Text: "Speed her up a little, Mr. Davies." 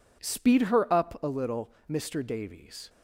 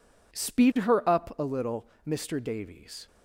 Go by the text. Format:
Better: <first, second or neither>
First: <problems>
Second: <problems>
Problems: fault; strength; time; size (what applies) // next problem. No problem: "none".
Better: neither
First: none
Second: none